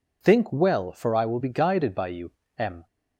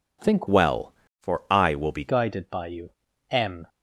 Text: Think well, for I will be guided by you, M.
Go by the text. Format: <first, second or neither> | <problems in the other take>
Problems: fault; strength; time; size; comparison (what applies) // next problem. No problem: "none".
first | changes voice from "well" to "be"; from 0.4 to 2.0 s; 1.6 s long